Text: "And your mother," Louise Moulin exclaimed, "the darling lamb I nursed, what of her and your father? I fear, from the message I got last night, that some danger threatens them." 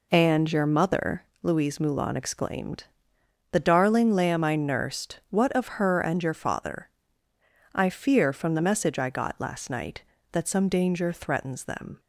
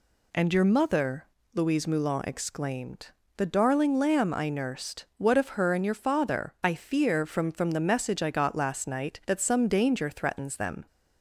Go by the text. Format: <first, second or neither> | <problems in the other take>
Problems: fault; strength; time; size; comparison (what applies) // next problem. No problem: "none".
first | says "from" twice; at 7.4 s